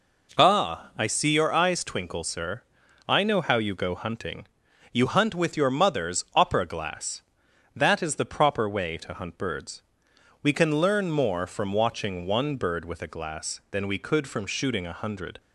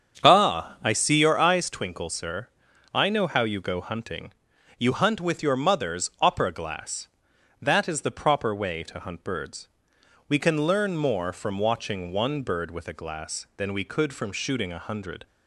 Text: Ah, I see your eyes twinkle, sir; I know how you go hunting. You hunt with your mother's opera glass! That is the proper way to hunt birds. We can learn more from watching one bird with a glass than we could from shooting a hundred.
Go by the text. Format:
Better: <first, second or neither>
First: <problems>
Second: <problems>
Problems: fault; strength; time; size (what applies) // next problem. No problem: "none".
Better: first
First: none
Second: starts louder than the rest; strong; until 1.7 s; 7.5 dB